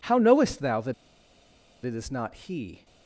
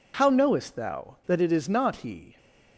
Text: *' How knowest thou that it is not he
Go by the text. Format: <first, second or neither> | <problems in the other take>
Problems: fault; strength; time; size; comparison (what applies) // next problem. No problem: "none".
second | pauses between "that" and "it"; noticeable; at 0.9 s; 0.90 s long